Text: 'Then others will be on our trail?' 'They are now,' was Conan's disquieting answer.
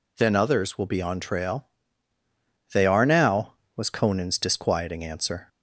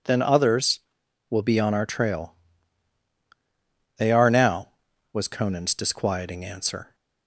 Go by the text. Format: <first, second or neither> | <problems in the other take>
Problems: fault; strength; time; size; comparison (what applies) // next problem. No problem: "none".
second | skips "our"; at 1.1 s